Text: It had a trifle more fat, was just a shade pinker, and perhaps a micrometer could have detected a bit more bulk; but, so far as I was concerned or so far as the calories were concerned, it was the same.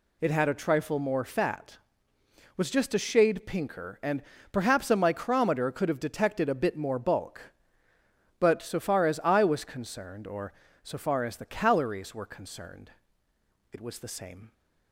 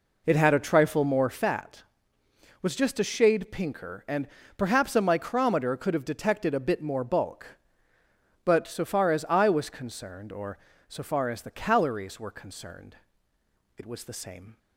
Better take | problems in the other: first | starts louder than the rest; noticeable; until 1.5 s; 4 dB // pauses between "and" and "perhaps"; slight; at 4.2 s; 0.28 s long; slight in the first

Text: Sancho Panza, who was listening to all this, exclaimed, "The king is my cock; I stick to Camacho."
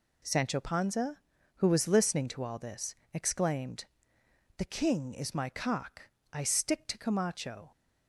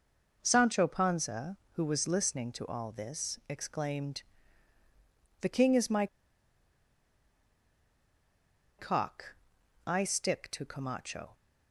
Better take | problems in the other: first | pauses between "my" and "cock"; strong; at 6.0 s; 2.7 s long

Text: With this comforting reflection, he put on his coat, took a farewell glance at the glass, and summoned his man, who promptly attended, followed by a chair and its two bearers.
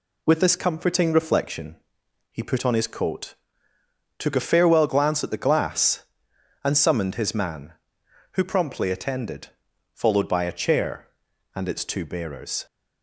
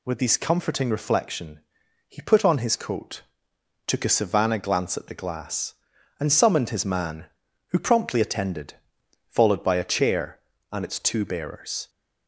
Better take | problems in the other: first | says "savannah" for "farewell"; at 4.0 s

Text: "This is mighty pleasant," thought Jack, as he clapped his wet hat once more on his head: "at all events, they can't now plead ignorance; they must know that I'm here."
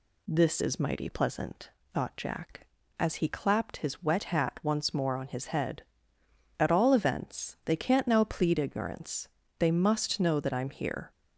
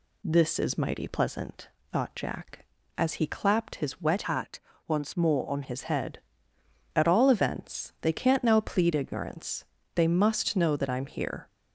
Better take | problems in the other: first | changes voice from "hat" to "on"; from 4.2 to 5.6 s; 1.4 s long // pauses between "hat" and "once"; slight; at 4.5 s; 0.28 s long

